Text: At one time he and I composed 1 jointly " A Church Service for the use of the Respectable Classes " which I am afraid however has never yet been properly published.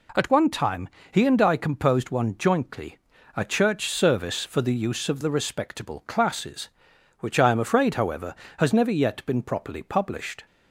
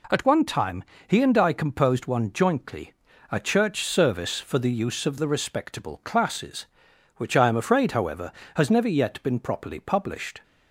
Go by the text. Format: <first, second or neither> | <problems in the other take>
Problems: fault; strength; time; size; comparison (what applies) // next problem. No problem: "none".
neither | pauses between "time" and "he"; slight; the same in both